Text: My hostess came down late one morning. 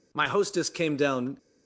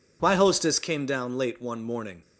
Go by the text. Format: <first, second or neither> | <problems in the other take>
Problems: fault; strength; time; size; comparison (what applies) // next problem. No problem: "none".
second | stops before "late one morning"; at 1.3 s